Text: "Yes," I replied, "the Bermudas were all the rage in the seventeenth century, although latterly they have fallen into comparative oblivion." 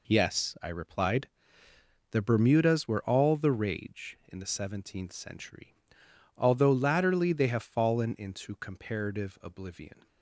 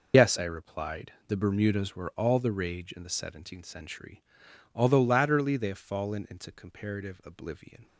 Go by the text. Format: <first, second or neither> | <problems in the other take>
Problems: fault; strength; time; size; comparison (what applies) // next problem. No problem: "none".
first | loses the start of "Yes"; at 0.1 s; 55 ms